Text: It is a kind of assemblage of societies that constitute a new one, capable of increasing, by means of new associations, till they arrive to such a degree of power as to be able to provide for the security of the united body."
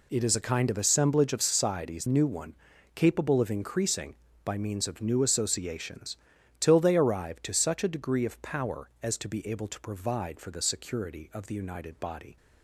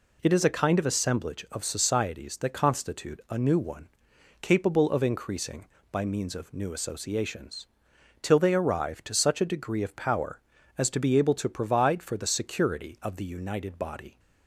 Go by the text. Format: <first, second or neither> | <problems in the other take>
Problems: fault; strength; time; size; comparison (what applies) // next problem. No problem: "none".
second | skips "that constitute a"; at 2.0 s